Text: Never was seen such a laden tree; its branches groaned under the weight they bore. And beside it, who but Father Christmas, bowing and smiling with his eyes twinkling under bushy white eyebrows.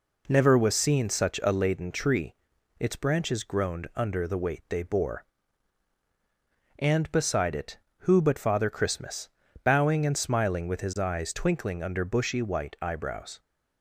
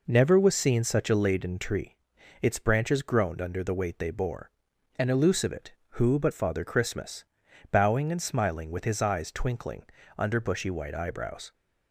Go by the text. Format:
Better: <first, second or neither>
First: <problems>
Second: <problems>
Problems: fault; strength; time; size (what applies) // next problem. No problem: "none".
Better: first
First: none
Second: says "elusive" for "beside"; at 5.0 s // pauses between "twinkling" and "under"; slight; at 9.8 s; 0.34 s long